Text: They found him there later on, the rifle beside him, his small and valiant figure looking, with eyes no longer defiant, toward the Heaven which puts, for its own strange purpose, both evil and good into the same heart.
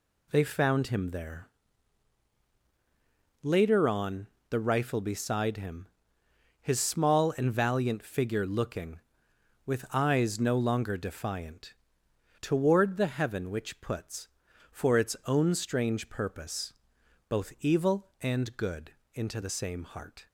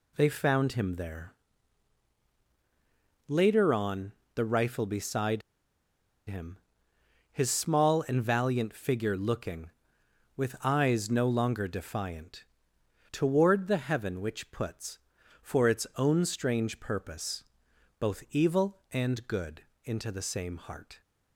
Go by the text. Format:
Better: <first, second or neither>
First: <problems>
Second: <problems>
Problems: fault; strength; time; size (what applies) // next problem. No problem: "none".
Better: first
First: pauses between "there" and "later"; strong; at 1.4 s; 1.9 s long // pauses between "good" and "into"; slight; at 18.9 s; 0.22 s long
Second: pauses between "there" and "later"; strong; at 1.3 s; 1.9 s long // pauses between "beside" and "him"; noticeable; at 5.4 s; 0.87 s long // pauses between "good" and "into"; slight; at 19.6 s; 0.22 s long